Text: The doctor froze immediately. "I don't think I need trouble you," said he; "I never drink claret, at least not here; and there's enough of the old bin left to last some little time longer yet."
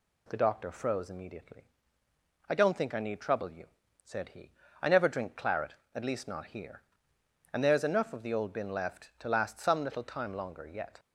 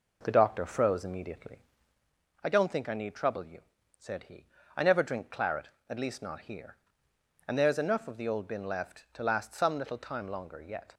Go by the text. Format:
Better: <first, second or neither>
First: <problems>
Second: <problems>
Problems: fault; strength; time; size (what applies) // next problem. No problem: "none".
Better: first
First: none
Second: starts louder than the rest; noticeable; until 2.1 s; 4.5 dB